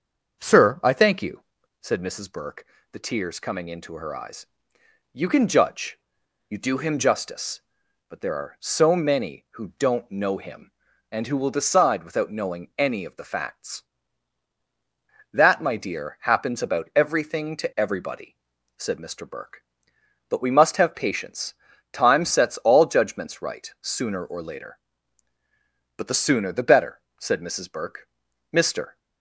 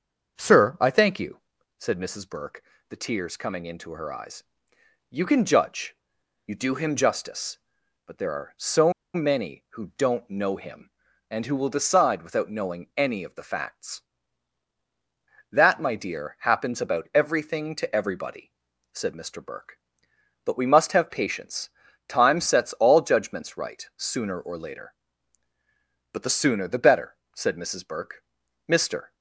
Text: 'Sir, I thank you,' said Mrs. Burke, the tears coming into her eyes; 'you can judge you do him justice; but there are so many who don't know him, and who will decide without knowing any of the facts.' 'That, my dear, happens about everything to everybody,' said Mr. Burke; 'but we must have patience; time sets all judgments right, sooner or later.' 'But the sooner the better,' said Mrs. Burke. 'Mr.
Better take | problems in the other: first | starts louder than the rest; until 1.8 s; 6.5 dB; also in the first // pauses between "judge" and "you"; noticeable; at 5.9 s; 0.52 s long; noticeable in the first // pauses between "so" and "many"; slight; at 8.9 s; 0.22 s long

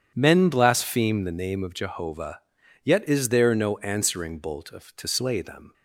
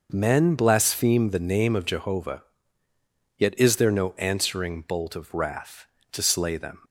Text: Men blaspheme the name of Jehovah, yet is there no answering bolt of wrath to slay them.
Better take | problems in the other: second | starts louder than the rest; strong; until 1.1 s; 8.5 dB // skips "wrath"; at 4.9 s

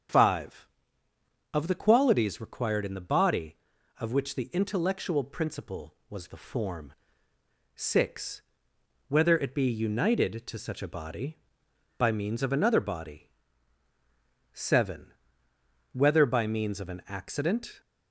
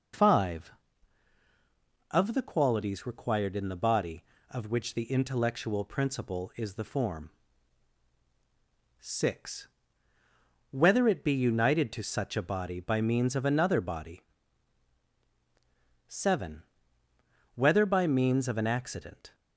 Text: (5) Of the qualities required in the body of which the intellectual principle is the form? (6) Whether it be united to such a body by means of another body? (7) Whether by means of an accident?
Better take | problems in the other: second | starts louder than the rest; strong; until 1.9 s; 7.5 dB // says "was" for "is"; at 6.0 s

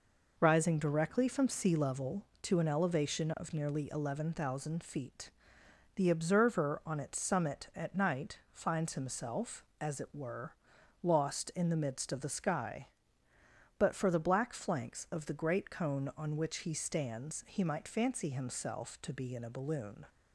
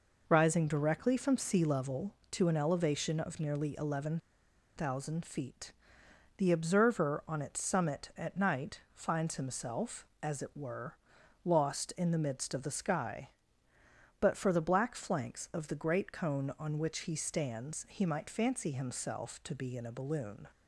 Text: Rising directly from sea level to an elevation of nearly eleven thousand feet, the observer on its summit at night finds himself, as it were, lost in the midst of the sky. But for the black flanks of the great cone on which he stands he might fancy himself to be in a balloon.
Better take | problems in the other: first | pauses between "eleven" and "thousand"; noticeable; at 4.1 s; 0.58 s long

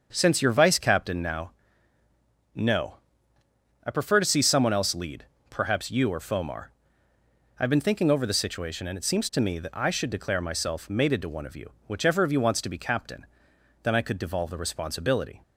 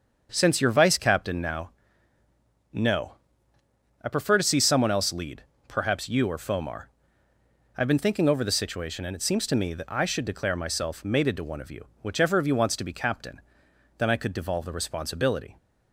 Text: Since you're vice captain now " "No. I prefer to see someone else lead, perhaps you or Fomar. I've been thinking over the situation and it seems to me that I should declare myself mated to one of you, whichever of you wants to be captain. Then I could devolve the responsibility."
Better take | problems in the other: neither | starts louder than the rest; the same in both

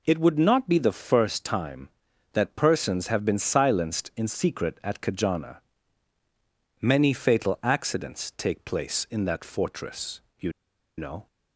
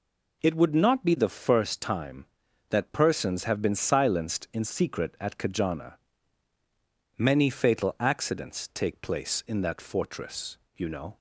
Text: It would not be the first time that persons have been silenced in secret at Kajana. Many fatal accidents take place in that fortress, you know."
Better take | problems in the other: second | pauses between "you" and "know"; noticeable; at 10.5 s; 0.46 s long

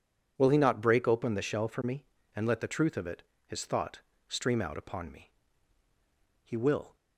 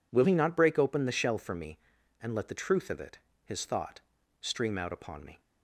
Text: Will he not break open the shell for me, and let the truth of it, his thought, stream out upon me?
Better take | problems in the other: second | goes on to say "He will"; from 6.4 s on; 0.52 s long

